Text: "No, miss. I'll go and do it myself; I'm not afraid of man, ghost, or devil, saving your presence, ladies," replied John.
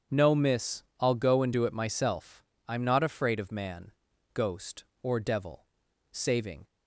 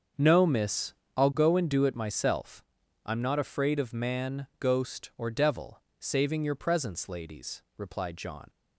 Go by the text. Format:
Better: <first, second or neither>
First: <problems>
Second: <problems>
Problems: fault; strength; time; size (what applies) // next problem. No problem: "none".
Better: second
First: starts louder than the rest; strong; until 1.2 s; 7.5 dB // stops before "your presence ladies replied John"; at 6.6 s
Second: starts louder than the rest; strong; until 1.4 s; 7 dB